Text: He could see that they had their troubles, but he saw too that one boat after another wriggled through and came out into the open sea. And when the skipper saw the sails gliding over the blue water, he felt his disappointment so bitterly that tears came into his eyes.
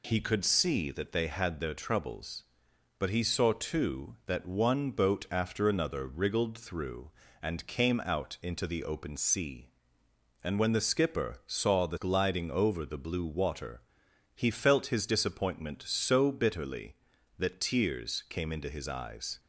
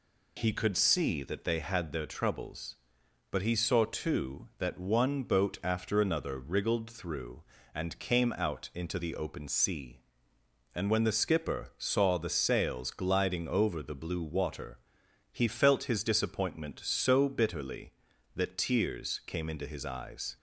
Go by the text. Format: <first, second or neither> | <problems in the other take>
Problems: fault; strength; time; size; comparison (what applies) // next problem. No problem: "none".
second | skips "sails"; at 11.9 s